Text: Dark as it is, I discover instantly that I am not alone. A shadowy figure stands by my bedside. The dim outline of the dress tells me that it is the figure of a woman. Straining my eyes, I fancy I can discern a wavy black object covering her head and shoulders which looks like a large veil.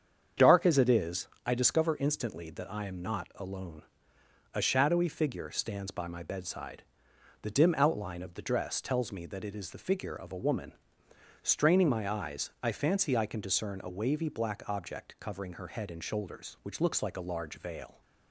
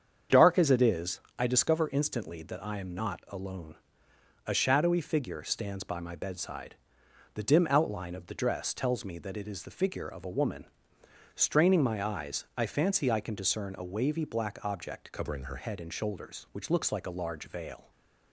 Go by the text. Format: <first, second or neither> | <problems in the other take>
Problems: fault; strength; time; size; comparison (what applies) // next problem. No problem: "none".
first | starts louder than the rest; strong; until 1.4 s; 7.5 dB; strong in the first // changes voice from "covering" to "her"; from 15.1 to 15.5 s; 0.4 s long // stays silent after the last word; slight; from 17.8 s on; 0.5 s long